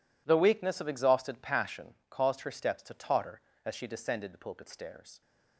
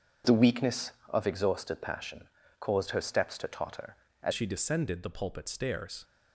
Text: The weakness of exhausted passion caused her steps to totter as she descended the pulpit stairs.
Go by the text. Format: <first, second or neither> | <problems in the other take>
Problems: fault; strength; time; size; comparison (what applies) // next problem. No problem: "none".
first | pauses between "passion" and "caused"; slight; at 2.2 s; 0.36 s long; slight in the first // changes voice at "she"; from 4.3 s on; 1.7 s long